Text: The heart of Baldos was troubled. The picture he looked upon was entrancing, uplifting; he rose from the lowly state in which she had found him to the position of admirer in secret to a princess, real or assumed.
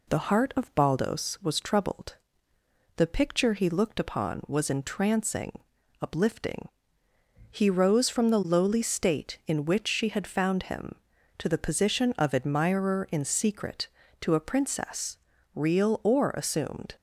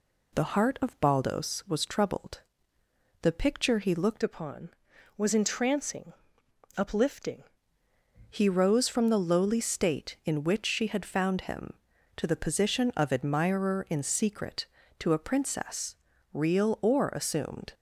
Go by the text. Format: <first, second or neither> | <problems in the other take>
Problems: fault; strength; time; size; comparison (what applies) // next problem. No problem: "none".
first | changes voice from "upon" to "uplifting"; from 4.2 to 7.4 s; 3.2 s long